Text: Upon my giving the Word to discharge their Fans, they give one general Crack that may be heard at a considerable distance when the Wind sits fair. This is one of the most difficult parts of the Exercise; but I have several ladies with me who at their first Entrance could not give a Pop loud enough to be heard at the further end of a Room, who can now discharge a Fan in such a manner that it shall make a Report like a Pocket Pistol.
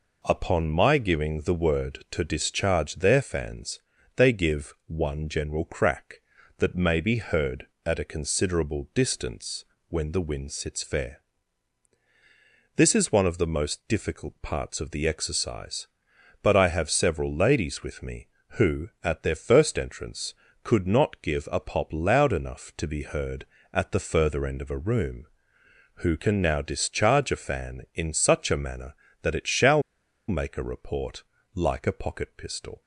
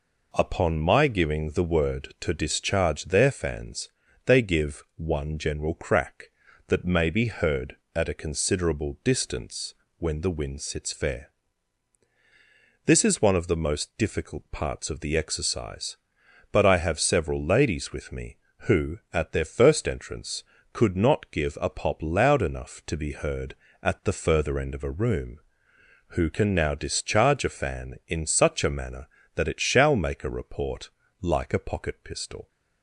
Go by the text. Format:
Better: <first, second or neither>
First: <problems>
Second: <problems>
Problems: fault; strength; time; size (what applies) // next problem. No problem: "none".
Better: second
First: pauses between "distance" and "when"; slight; at 9.6 s; 0.24 s long // pauses between "shall" and "make"; noticeable; at 29.8 s; 0.48 s long // pauses between "Report" and "like"; slight; at 31.2 s; 0.32 s long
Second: pauses between "distance" and "when"; slight; at 9.7 s; 0.24 s long // pauses between "Report" and "like"; slight; at 30.8 s; 0.32 s long